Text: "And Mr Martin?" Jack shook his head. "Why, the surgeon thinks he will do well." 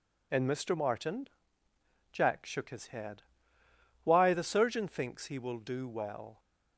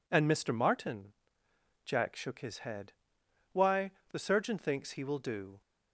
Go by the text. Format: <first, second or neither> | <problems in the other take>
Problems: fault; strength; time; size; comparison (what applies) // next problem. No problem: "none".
first | stops before "well"; at 5.6 s